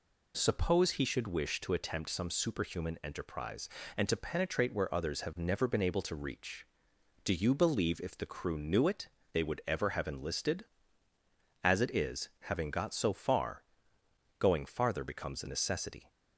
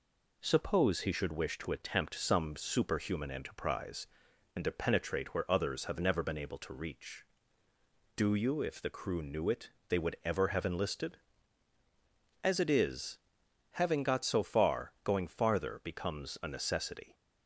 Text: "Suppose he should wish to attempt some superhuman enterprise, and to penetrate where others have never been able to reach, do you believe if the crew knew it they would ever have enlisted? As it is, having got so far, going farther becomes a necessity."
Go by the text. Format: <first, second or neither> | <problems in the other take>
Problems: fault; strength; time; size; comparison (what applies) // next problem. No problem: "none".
first | skips "believe"; at 8.6 s // pauses between "it" and "they"; slight; at 9.7 s; 0.18 s long; slight in the first